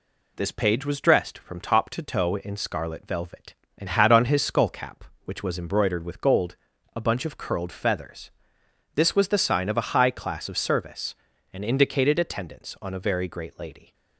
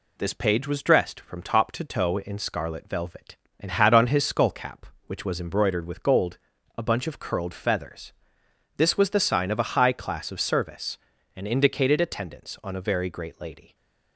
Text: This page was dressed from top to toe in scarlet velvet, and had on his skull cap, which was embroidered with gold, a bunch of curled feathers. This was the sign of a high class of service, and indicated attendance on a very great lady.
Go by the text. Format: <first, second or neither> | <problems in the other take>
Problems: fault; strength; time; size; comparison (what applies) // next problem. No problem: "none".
neither | none